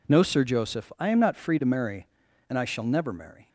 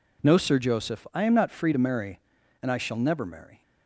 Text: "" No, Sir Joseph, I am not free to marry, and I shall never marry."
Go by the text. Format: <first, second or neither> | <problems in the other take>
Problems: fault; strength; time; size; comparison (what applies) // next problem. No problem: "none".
neither | none